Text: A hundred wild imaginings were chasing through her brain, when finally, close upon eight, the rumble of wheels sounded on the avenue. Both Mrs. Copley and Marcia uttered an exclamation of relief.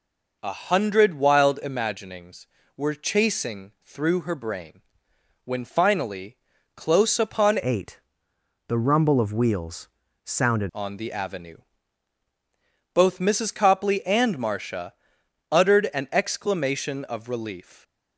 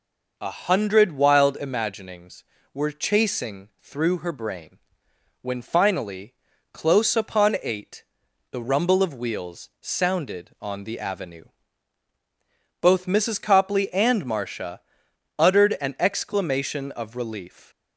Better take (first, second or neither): second